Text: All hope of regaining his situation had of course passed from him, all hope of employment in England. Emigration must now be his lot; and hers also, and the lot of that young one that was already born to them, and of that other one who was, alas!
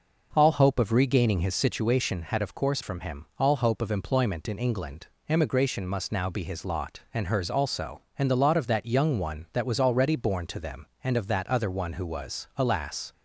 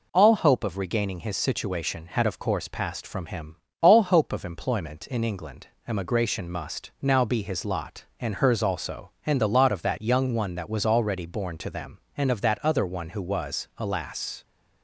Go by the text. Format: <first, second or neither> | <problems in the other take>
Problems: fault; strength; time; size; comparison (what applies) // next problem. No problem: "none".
second | skips "passed"; at 2.8 s